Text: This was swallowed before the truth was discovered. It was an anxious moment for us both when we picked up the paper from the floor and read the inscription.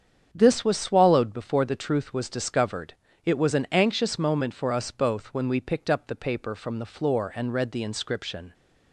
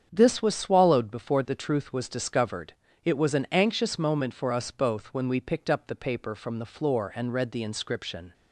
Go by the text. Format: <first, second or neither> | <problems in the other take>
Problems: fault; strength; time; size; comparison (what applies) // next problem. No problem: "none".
neither | starts louder than the rest; strong; the same in both